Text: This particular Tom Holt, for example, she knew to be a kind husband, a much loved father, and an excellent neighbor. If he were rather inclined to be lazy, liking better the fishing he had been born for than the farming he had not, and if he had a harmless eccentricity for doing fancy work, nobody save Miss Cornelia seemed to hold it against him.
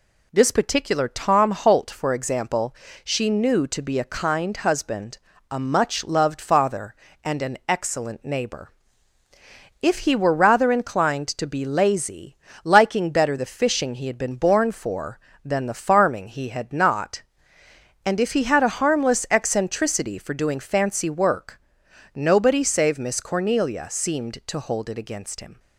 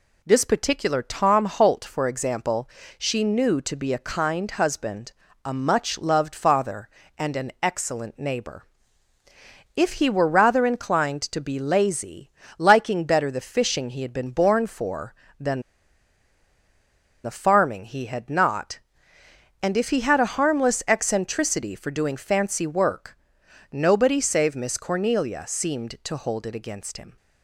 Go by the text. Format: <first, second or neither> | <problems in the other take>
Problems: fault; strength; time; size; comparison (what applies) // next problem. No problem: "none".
first | pauses between "than" and "the"; strong; at 15.6 s; 1.6 s long